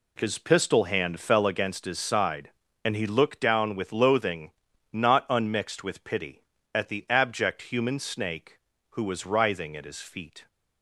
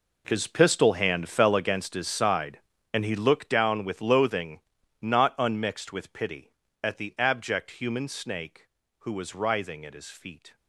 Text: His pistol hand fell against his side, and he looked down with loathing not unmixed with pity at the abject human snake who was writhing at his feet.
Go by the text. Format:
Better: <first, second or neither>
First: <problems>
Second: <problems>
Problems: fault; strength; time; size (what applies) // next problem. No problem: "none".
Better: first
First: pauses between "loathing" and "not"; at 4.5 s; 0.42 s long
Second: gets quieter; strong; throughout; 15 dB // pauses between "loathing" and "not"; at 4.5 s; 0.42 s long